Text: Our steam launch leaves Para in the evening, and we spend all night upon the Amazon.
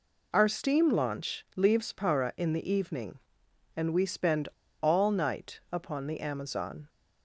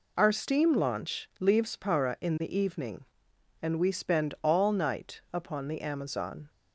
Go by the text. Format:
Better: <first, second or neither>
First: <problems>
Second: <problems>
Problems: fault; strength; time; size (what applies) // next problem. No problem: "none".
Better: second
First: pauses between "spend" and "all"; slight; at 4.4 s; 0.32 s long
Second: none